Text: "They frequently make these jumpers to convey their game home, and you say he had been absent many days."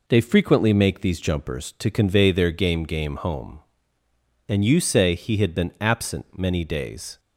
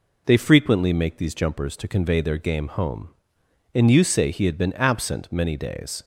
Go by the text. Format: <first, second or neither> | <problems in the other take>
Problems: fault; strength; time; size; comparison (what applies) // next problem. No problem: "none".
second | says "game" twice; at 2.8 s